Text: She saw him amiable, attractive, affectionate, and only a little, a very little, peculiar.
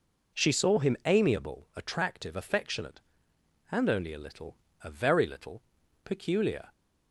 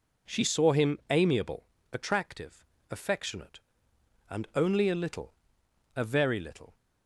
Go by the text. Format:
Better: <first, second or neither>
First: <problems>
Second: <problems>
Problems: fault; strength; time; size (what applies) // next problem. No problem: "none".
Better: first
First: none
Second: stops before "peculiar"; at 6.7 s